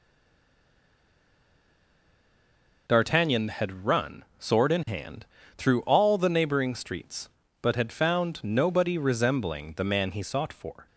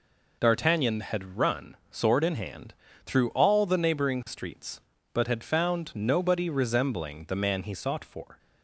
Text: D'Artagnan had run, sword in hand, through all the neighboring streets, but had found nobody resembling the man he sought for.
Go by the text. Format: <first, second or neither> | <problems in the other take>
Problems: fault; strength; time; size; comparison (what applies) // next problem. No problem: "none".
second | stays silent before the first word; strong; until 2.8 s; 2.8 s long